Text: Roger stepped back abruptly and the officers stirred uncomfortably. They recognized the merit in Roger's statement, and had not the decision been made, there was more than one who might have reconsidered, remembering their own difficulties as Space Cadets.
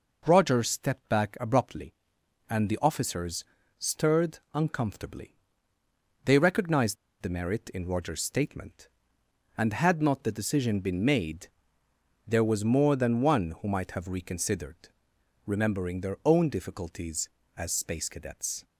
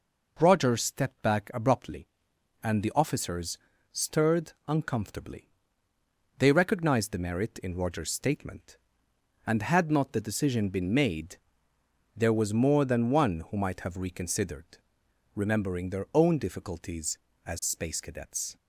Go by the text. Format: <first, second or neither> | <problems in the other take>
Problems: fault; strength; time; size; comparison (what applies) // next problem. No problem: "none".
second | pauses between "officers" and "stirred"; slight; at 3.4 s; 0.34 s long; slight in the second // pauses between "stirred" and "uncomfortably"; slight; at 4.3 s; 0.16 s long; slight in the second // pauses between "recognized" and "the"; slight; at 6.9 s; 0.26 s long